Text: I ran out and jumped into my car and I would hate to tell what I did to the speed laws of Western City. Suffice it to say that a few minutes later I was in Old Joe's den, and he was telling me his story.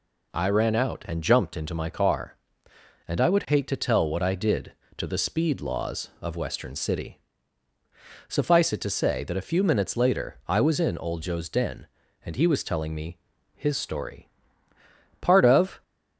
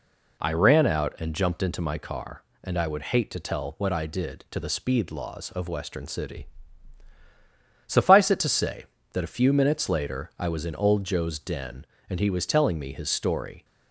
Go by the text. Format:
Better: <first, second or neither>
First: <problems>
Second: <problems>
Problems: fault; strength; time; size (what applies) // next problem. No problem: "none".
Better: second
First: pauses between "me" and "his"; slight; at 13.1 s; 0.36 s long // goes on to say "Part of"; noticeable; from 15.2 s on; 0.62 s long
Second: none